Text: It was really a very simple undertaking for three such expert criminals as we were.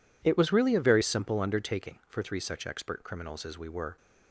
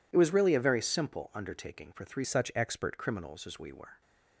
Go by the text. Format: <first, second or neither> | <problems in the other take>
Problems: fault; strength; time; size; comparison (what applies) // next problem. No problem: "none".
first | changes voice from "such" to "expert"; from 2.2 to 2.9 s; 0.7 s long